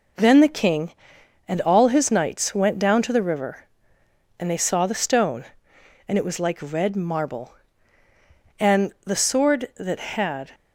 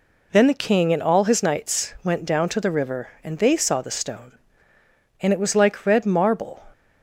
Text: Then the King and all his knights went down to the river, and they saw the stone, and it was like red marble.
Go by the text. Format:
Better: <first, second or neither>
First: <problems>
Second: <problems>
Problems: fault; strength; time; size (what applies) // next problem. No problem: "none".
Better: second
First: goes on to say "And the sword that had"; strong; from 8.5 s on; 1.9 s long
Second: none